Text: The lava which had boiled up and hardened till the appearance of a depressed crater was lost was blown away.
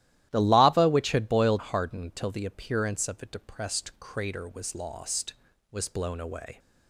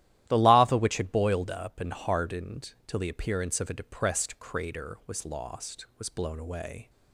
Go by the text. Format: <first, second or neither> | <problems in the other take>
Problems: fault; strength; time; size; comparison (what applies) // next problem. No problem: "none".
second | starts louder than the rest; strong; until 1.3 s; 14 dB; strong in the second // skips "up and"; at 1.5 s